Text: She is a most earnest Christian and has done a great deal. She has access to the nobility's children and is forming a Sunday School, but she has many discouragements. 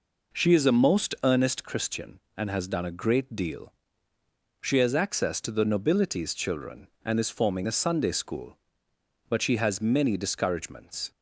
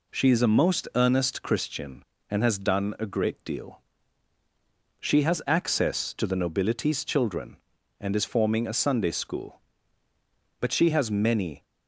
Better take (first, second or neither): first